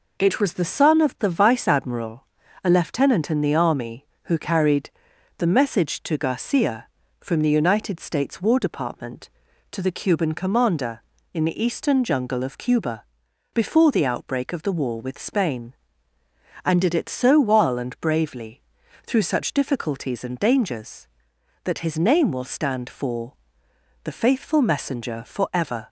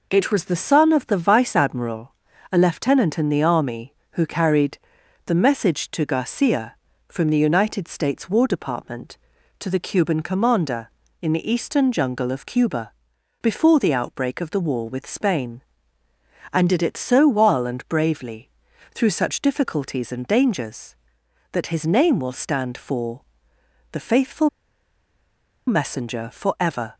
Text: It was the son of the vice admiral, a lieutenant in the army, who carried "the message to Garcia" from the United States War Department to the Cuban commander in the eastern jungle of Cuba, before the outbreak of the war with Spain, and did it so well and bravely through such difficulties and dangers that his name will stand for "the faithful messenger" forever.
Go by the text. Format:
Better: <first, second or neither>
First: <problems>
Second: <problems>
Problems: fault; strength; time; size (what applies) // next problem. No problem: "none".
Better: first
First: pauses between "carried" and "the"; noticeable; at 4.9 s; 0.48 s long // pauses between "bravely" and "through"; noticeable; at 18.6 s; 0.46 s long // pauses between "for" and "the"; noticeable; at 23.3 s; 0.70 s long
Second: pauses between "carried" and "the"; noticeable; at 4.7 s; 0.48 s long // pauses between "bravely" and "through"; noticeable; at 18.4 s; 0.46 s long // pauses between "for" and "the"; noticeable; at 23.2 s; 0.70 s long // pauses between "faithful" and "messenger"; at 24.4 s; 1.1 s long